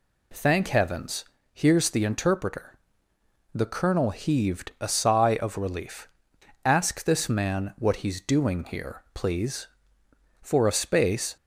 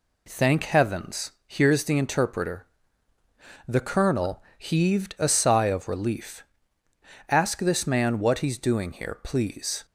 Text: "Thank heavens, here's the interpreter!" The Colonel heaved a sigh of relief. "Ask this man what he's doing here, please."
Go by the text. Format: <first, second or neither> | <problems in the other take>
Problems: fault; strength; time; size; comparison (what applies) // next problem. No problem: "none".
second | goes on to say "For a space"; noticeable; from 10.3 s on; 0.96 s long